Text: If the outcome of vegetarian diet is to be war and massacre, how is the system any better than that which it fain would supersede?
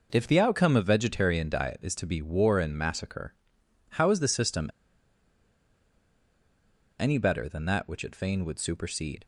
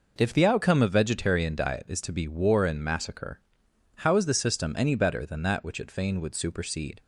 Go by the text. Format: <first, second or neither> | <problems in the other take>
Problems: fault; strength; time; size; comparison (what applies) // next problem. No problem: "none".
second | pauses between "system" and "any"; strong; at 4.6 s; 2.3 s long